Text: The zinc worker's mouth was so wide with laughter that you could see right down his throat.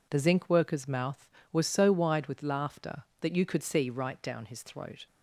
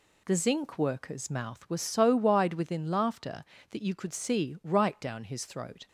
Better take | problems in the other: first | says "within" for "with"; at 2.5 s

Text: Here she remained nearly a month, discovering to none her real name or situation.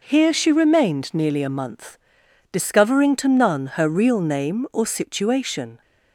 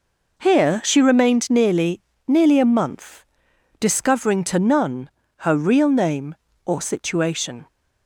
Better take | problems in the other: first | says "nearly" twice; at 2.2 s // pauses between "none" and "her"; slight; at 5.0 s; 0.28 s long

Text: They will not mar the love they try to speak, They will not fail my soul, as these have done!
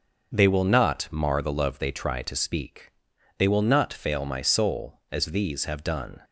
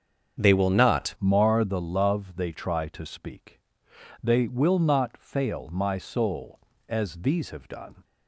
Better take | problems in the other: first | starts louder than the rest; strong; until 1.4 s; 7.5 dB; also in the first // changes voice at "mar"; from 1.1 s on; 6.9 s long

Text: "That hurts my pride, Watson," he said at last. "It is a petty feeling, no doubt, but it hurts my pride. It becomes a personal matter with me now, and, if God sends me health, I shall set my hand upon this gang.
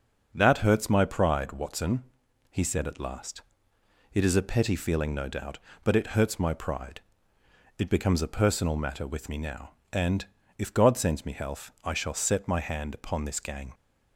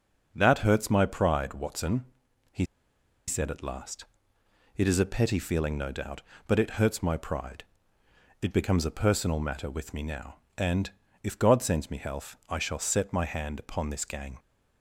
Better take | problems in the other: first | starts louder than the rest; noticeable; until 1.3 s; 6 dB; also in the first // pauses between "he" and "said"; noticeable; at 2.6 s; 0.64 s long

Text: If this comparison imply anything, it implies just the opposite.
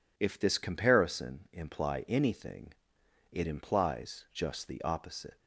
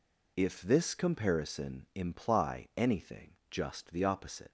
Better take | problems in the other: first | skips "it implies"; at 3.4 s

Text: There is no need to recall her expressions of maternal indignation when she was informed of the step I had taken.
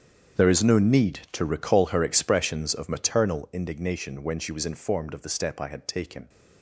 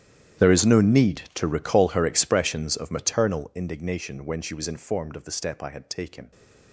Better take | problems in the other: first | gets quieter; strong; throughout; 21 dB // starts louder than the rest; strong; until 1.5 s; 11 dB; strong in the first

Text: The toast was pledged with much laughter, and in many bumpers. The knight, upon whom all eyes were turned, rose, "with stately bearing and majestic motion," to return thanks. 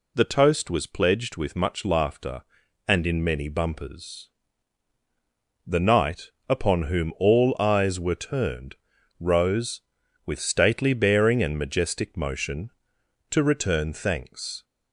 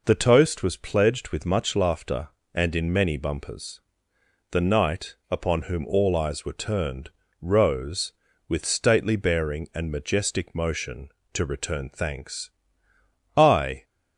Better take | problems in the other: first | goes on to say "I"; slight; from 13.3 s on; 0.46 s long

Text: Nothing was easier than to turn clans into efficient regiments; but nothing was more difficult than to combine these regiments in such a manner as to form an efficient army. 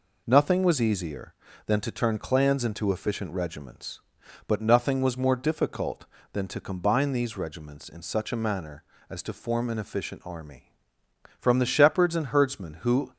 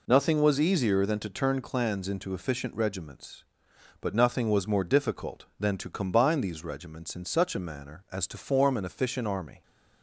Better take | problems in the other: second | goes on to say "From the shepherds and herdsmen who"; strong; from 11.3 s on; 1.7 s long

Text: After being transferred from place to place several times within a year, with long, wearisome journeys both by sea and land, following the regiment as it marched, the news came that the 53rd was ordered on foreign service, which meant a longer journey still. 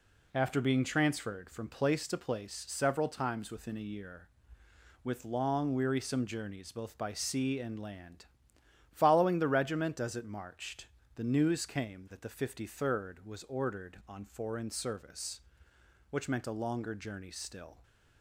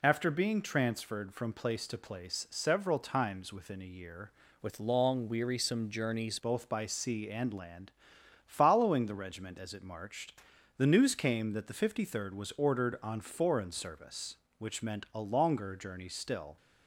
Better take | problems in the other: first | changes voice from "with" to "journeys"; from 4.6 to 6.3 s; 1.7 s long

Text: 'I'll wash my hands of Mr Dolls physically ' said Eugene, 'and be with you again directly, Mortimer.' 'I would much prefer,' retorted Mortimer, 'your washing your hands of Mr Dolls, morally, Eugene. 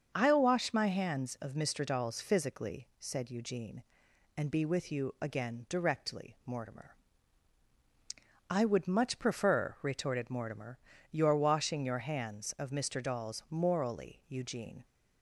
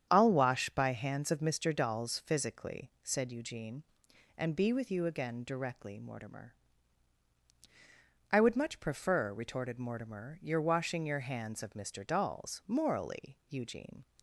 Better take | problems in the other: first | starts louder than the rest; strong; until 1.1 s; 8.5 dB; also in the first // says "by" for "my"; at 0.6 s

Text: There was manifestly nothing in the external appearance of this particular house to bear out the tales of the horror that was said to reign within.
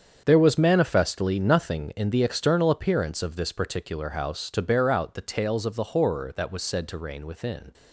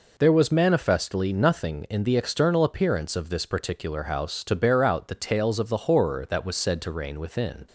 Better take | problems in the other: second | gets quieter; strong; throughout; 12 dB

